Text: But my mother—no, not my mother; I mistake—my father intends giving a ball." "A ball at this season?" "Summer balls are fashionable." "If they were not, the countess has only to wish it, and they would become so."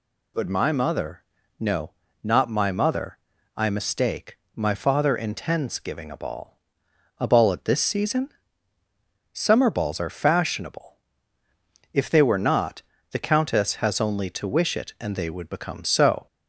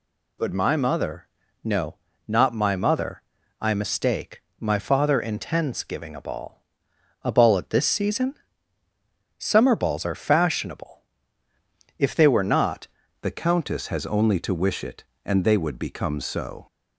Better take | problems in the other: first | changes voice at "the"; from 13.2 s on; 3.4 s long

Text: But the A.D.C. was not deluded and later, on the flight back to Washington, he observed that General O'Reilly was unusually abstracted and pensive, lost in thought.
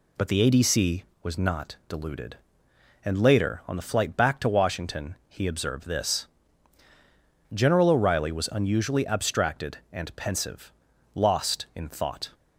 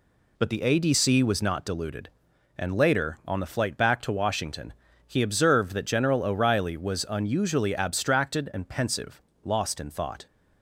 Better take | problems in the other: second | says "this" for "that"; at 5.8 s

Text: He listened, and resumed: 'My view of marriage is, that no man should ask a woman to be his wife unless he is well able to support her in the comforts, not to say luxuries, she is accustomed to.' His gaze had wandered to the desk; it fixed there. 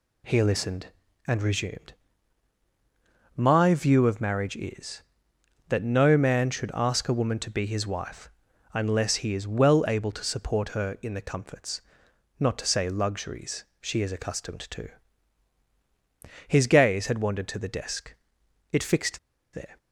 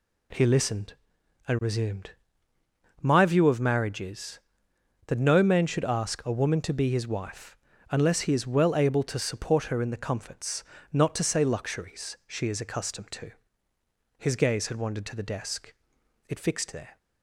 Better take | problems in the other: second | pauses between "wife" and "unless"; at 8.3 s; 0.42 s long; slight in the second // pauses between "fixed" and "there"; slight; at 19.1 s; 0.34 s long

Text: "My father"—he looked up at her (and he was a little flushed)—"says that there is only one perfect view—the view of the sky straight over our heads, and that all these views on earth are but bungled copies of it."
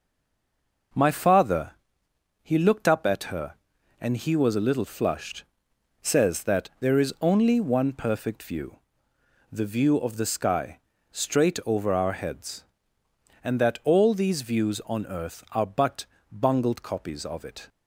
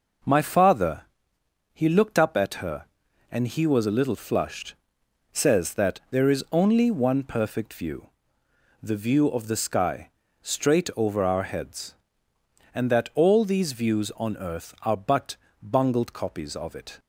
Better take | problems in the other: second | stays silent before the first word; slight; until 0.9 s; 0.9 s long // starts louder than the rest; until 2.6 s; 6 dB; also in the second // pauses between "sky" and "straight"; slight; at 10.8 s; 0.32 s long; slight in the second // pauses between "but" and "bungled"; slight; at 16.0 s; 0.26 s long; slight in the second

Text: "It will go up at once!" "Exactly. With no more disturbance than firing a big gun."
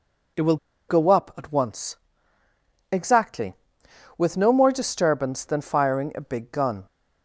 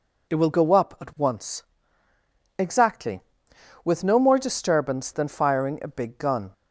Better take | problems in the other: second | pauses between "will" and "go"; slight; at 0.5 s; 0.33 s long

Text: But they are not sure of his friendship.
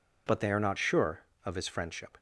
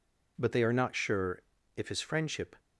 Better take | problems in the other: first | says "if" for "of"; at 1.7 s

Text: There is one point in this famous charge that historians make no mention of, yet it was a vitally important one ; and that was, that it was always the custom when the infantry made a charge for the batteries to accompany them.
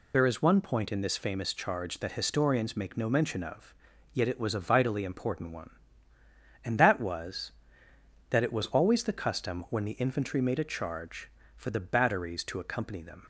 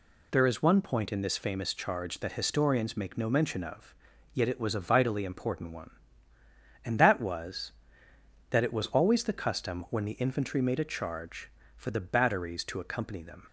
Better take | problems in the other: second | loses the start of "There"; at 0.1 s; 30 ms

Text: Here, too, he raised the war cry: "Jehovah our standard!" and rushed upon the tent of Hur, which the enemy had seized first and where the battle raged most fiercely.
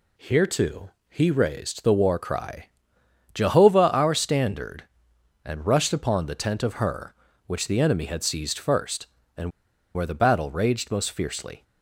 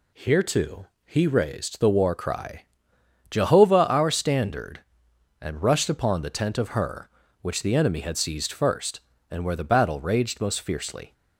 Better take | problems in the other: second | pauses between "and" and "where"; at 9.5 s; 0.44 s long

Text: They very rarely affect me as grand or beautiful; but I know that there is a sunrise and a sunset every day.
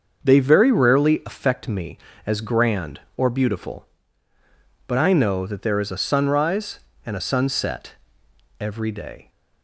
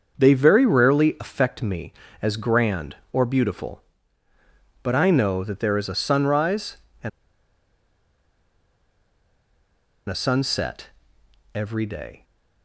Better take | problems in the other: first | starts louder than the rest; until 1.1 s; 6.5 dB; also in the first // pauses between "and" and "a"; strong; at 7.0 s; 2.9 s long // pauses between "sunset" and "every"; noticeable; at 10.8 s; 0.66 s long; noticeable in the first

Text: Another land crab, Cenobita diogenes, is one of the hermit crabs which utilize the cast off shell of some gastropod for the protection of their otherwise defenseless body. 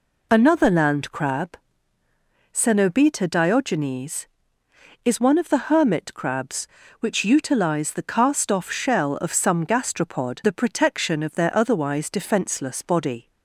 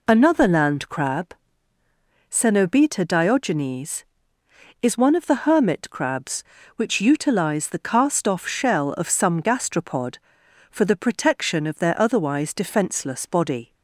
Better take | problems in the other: second | skips "for"; at 10.4 s

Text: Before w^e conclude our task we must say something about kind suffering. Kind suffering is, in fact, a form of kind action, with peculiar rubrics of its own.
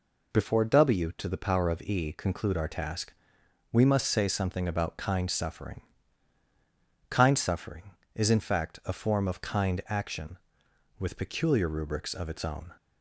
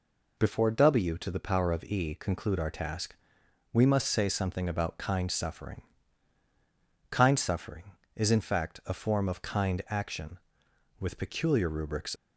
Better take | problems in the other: first | pauses between "task" and "we"; noticeable; at 3.1 s; 0.56 s long; noticeable in the first // stops before "of its own"; at 12.1 s

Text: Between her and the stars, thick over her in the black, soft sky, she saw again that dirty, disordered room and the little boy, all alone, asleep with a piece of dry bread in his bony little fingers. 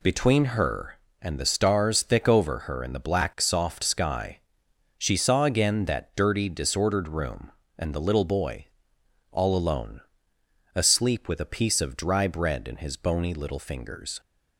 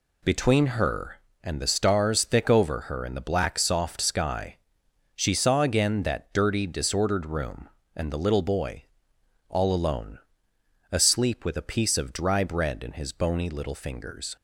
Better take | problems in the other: neither | none

